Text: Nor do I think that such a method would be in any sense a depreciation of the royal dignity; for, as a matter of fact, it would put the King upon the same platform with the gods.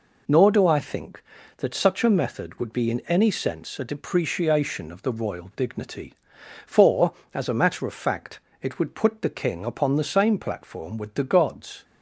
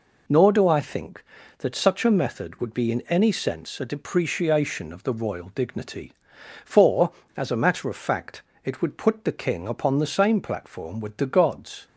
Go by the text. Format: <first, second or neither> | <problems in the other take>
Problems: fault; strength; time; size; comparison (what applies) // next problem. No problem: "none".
neither | none